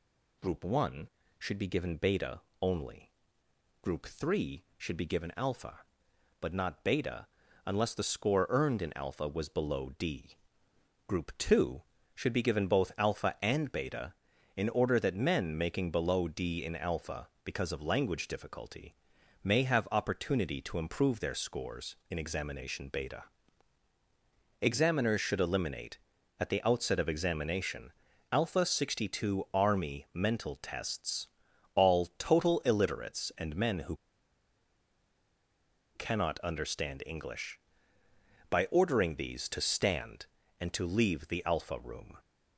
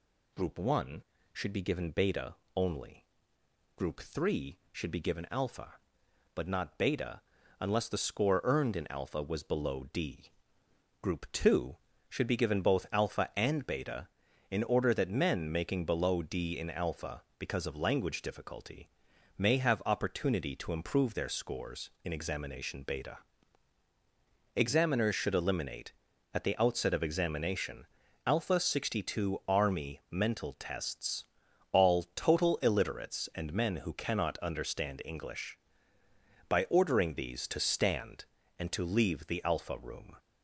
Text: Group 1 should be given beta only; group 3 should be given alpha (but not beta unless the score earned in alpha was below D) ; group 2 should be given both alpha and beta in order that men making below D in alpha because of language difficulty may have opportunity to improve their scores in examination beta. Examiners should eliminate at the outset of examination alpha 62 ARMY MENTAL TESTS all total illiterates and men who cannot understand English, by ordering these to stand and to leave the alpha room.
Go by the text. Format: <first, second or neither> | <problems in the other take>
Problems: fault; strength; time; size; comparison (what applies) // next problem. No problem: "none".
second | pauses between "beta" and "only"; slight; at 2.4 s; 0.22 s long; slight in the second // pauses between "beta" and "unless"; at 7.2 s; 0.40 s long; also in the second // pauses between "difficulty" and "may"; noticeable; at 18.9 s; 0.48 s long; noticeable in the second // pauses between "examination" and "alpha"; at 27.9 s; 0.40 s long; also in the second // pauses between "TESTS" and "all"; noticeable; at 31.2 s; 0.46 s long; noticeable in the second // pauses between "who" and "cannot"; strong; at 33.9 s; 2.0 s long